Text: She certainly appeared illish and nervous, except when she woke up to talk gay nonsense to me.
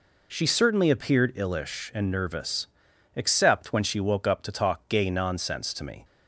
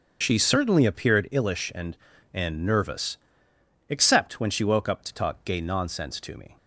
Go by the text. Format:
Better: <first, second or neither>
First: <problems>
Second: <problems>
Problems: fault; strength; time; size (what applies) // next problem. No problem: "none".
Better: first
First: none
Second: starts louder than the rest; until 1.2 s; 6.5 dB // says "and" twice; at 2.3 s